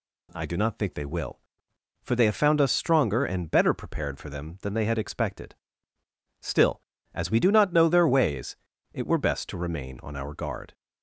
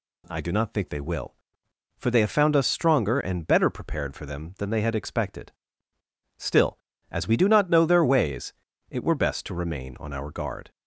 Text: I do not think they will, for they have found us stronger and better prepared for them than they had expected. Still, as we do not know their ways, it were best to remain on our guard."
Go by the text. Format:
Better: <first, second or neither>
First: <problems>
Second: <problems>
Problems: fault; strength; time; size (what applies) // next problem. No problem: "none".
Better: neither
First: none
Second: none